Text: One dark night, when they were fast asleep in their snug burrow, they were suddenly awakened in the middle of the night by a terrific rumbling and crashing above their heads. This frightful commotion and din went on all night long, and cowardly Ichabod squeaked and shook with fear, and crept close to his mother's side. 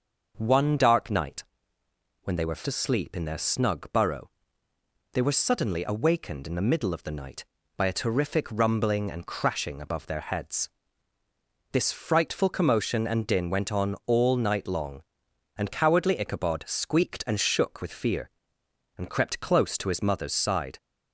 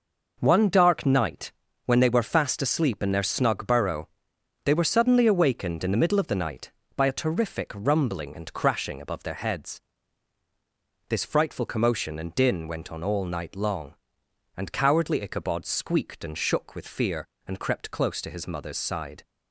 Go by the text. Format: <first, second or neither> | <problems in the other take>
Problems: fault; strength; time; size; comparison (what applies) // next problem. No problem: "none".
second | starts louder than the rest; noticeable; until 1.3 s; 6 dB // skips "fast"; at 2.6 s